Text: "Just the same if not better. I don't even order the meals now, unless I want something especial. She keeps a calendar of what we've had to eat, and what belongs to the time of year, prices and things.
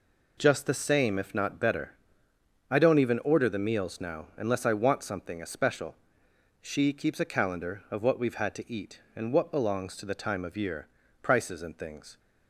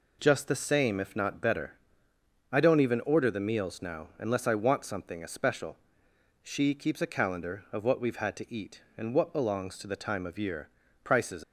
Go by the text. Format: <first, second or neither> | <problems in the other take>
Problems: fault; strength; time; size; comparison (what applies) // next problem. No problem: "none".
first | stops before "and things"; at 11.4 s